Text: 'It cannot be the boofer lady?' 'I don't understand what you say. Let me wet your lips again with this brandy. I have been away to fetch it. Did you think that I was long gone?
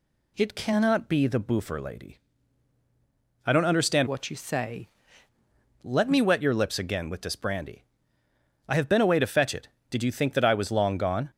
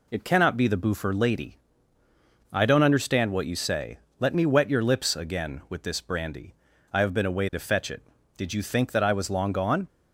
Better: second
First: changes voice from "what" to "say"; from 4.0 to 4.8 s; 0.8 s long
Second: none

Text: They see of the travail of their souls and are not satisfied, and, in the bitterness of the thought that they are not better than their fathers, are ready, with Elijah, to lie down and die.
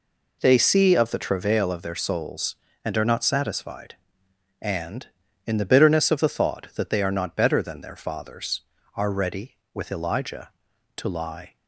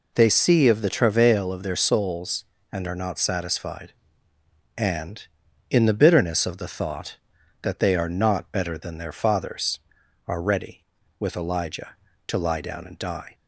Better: second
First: stops before "down and die"; at 11.5 s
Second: none

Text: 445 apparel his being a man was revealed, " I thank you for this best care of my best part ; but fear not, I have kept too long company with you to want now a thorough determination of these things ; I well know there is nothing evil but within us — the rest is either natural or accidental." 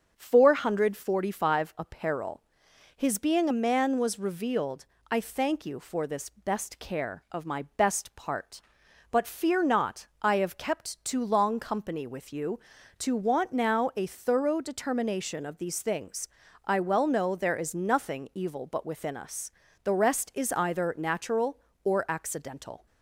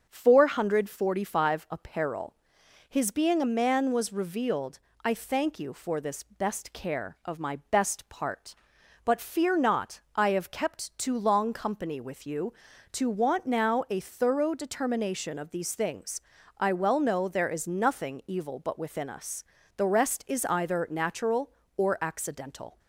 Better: neither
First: starts louder than the rest; strong; until 1.1 s; 7 dB // pauses between "apparel" and "his"; noticeable; at 2.4 s; 0.56 s long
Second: starts louder than the rest; strong; until 1.1 s; 7 dB // pauses between "apparel" and "his"; noticeable; at 2.3 s; 0.56 s long

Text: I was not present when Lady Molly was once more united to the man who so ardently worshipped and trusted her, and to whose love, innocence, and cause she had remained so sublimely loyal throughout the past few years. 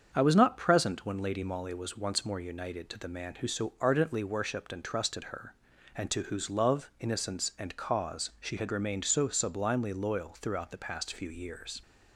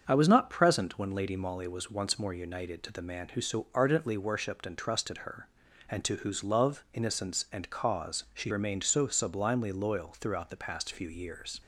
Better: first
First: starts louder than the rest; until 1.1 s; 7 dB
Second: starts louder than the rest; strong; until 1.0 s; 7 dB // skips "had"; at 8.5 s

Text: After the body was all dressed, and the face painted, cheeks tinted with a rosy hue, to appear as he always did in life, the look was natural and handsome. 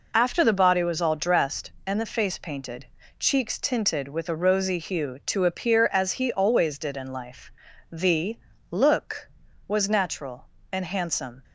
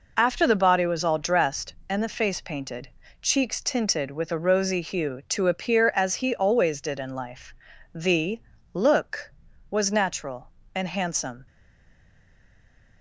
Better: first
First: pauses between "the" and "look"; slight; at 8.3 s; 0.32 s long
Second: pauses between "the" and "look"; slight; at 8.4 s; 0.32 s long // stays silent after the last word; noticeable; from 11.4 s on; 1.6 s long

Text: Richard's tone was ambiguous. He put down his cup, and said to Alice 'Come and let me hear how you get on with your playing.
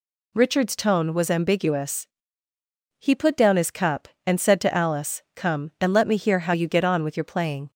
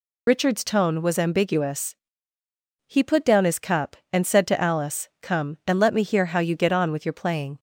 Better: first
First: none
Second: loses the start of "Richard's"; at 0.2 s; 45 ms

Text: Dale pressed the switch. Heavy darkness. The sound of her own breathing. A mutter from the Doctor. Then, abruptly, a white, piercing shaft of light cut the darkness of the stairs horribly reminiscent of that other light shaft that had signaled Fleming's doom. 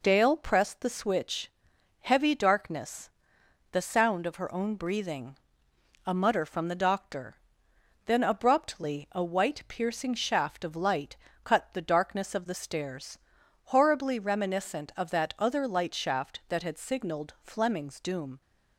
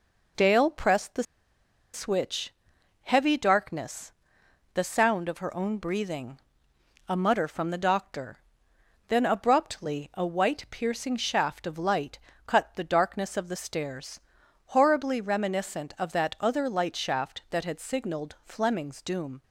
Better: first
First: pauses between "light" and "cut"; slight; at 11.1 s; 0.28 s long // pauses between "stairs" and "horribly"; noticeable; at 13.1 s; 0.48 s long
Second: pauses between "the" and "switch"; noticeable; at 1.2 s; 0.69 s long // pauses between "light" and "cut"; slight; at 12.1 s; 0.28 s long // pauses between "stairs" and "horribly"; noticeable; at 14.2 s; 0.48 s long

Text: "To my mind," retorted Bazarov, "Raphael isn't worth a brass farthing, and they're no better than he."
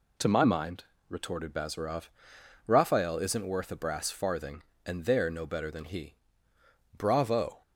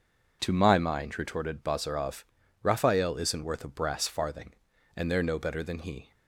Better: second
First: goes on to say "Bravo"; noticeable; from 6.9 s on; 0.64 s long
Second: none

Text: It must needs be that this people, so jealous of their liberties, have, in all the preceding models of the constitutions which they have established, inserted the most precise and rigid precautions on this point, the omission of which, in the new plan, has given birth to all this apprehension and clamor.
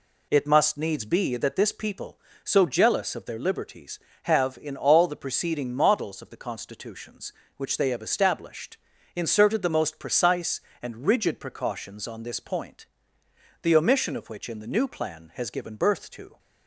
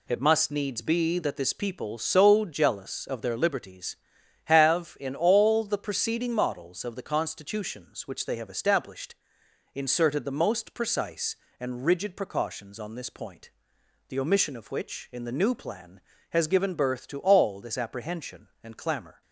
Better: second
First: stops before "all this apprehension and clamor"; at 16.3 s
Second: none

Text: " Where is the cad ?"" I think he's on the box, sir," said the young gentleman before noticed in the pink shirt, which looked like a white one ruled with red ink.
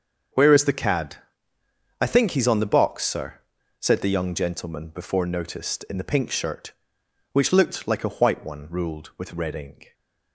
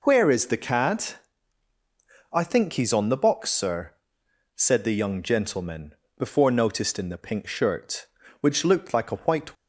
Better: first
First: none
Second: pauses between "gentleman" and "before"; slight; at 5.9 s; 0.24 s long // stops before "one ruled with red ink"; at 9.5 s

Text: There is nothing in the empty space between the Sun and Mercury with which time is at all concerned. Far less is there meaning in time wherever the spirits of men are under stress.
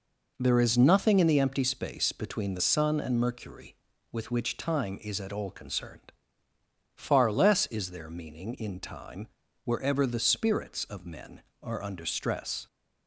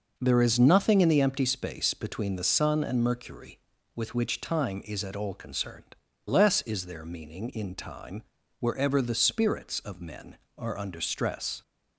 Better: first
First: pauses between "time" and "wherever"; at 9.2 s; 0.38 s long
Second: skips "Far"; at 6.1 s // pauses between "time" and "wherever"; at 8.2 s; 0.38 s long

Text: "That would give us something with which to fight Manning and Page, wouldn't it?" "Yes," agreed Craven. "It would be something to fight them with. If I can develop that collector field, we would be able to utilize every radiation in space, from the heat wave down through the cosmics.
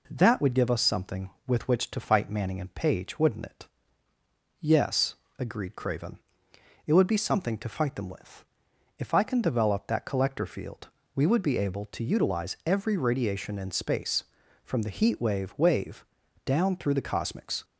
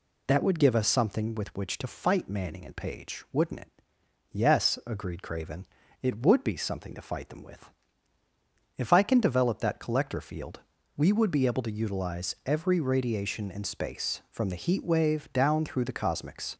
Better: second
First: says "wave" twice; at 15.5 s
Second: none

